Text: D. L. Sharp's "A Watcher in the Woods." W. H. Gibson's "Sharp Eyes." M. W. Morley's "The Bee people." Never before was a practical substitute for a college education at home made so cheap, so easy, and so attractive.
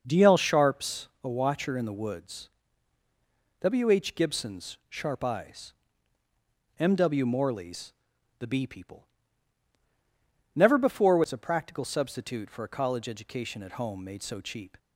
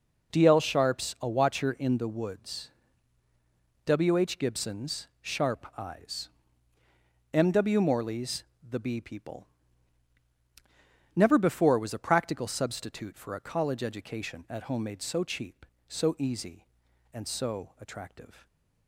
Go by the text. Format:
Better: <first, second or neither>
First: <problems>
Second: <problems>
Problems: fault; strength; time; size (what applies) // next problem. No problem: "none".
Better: second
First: starts louder than the rest; noticeable; until 1.0 s; 6 dB // pauses between "Sharp's" and "A"; slight; at 1.0 s; 0.16 s long // pauses between "Morley's" and "The"; noticeable; at 7.9 s; 0.46 s long // stops before "so easy and so attractive"; at 14.7 s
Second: pauses between "Morley's" and "The"; slight; at 8.4 s; 0.26 s long